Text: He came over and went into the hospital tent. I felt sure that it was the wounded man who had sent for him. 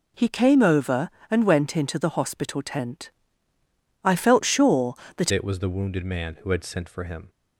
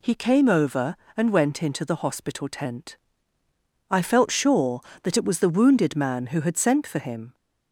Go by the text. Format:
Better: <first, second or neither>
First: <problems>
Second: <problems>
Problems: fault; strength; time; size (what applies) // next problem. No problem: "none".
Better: second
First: changes voice at "it"; from 5.3 s on; 1.9 s long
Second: none